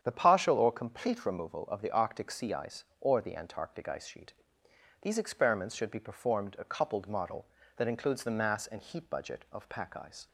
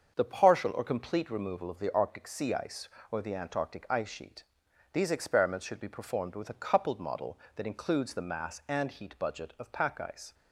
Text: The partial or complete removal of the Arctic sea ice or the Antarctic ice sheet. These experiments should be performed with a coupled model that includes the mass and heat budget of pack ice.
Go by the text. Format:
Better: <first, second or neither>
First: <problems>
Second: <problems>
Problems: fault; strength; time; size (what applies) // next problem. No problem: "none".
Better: second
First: starts louder than the rest; strong; until 1.0 s; 8.5 dB // skips "with"; at 6.5 s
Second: starts louder than the rest; until 1.1 s; 7 dB